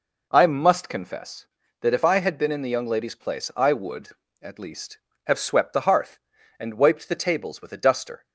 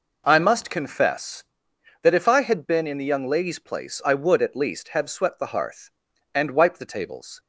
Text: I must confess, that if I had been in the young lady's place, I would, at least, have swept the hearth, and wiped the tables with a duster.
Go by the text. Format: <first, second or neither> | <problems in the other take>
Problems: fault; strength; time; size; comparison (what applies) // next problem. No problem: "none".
first | stops before "with a duster"; at 7.3 s